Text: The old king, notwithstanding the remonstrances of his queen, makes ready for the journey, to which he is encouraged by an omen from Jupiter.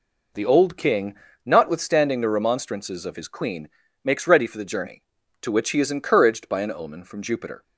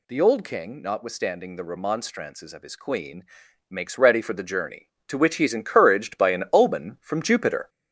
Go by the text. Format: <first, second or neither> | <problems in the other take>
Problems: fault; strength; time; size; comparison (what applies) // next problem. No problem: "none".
first | gets louder; noticeable; throughout; 5 dB